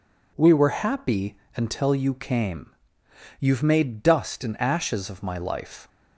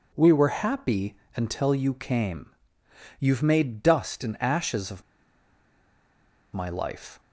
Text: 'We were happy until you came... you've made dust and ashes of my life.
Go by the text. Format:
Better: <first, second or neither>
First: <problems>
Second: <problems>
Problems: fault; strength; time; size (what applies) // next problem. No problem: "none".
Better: first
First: pauses between "happy" and "until"; slight; at 1.3 s; 0.18 s long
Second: pauses between "happy" and "until"; slight; at 1.1 s; 0.18 s long // pauses between "of" and "my"; strong; at 5.0 s; 1.5 s long